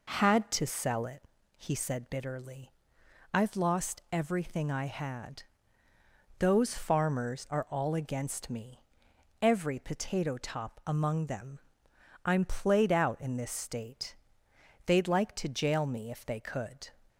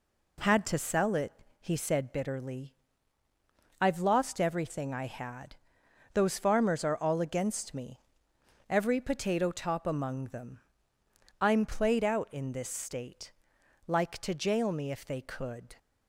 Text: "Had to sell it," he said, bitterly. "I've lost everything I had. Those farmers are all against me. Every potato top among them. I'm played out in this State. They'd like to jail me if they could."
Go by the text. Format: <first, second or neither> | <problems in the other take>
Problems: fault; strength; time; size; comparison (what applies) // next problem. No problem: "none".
first | skips "They'd"; at 13.5 s